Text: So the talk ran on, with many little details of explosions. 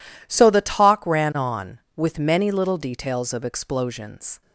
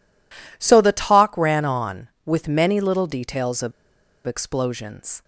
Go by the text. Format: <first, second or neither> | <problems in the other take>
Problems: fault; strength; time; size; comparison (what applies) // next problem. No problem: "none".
first | pauses between "of" and "explosions"; noticeable; at 3.7 s; 0.56 s long